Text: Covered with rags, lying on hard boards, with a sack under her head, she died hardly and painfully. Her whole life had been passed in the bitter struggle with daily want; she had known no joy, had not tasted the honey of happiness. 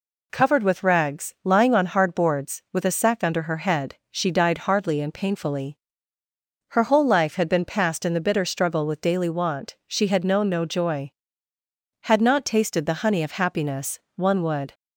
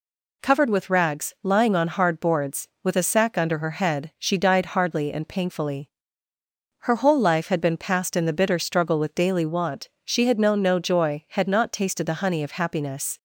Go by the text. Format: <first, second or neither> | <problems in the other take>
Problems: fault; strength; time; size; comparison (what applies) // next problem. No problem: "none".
second | goes on to say "One would"; from 14.1 s on; 0.58 s long